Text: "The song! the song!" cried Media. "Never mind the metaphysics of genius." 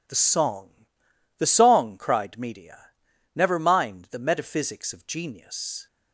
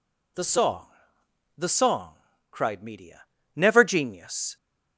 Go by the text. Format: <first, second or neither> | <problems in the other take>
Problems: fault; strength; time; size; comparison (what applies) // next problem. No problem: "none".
first | skips "mind the metaphysics of"; at 3.8 s